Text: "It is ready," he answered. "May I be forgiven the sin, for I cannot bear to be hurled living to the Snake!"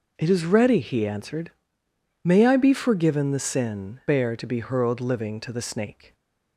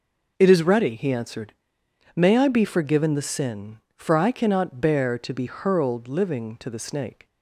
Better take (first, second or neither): second